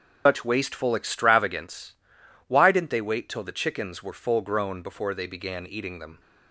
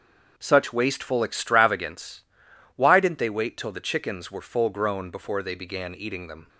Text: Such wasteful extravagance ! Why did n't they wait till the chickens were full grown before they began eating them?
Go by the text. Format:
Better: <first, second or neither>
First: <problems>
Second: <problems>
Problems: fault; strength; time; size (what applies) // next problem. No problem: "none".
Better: second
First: loses the start of "Such"; at 0.2 s; 155 ms // starts louder than the rest; until 1.2 s; 6.5 dB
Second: starts louder than the rest; until 1.3 s; 7 dB